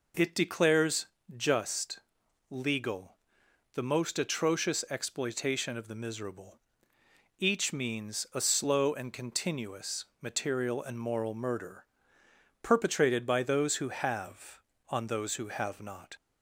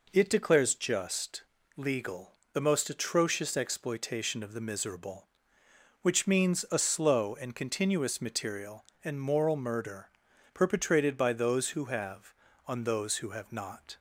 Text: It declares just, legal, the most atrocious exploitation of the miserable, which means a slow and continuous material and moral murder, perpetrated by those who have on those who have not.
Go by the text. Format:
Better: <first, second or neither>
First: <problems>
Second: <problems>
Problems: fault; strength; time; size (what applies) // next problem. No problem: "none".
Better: second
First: pauses between "declares" and "just"; slight; at 1.0 s; 0.28 s long // says "each" for "which"; at 7.3 s // pauses between "continuous" and "material"; slight; at 10.0 s; 0.16 s long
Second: none